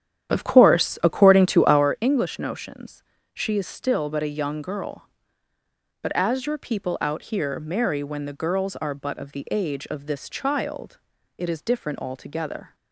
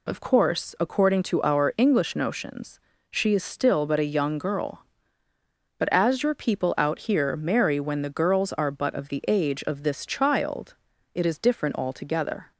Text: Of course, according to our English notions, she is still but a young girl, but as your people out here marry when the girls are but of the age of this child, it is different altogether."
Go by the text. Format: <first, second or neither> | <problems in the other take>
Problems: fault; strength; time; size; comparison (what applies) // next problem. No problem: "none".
second | starts louder than the rest; strong; until 2.0 s; 10 dB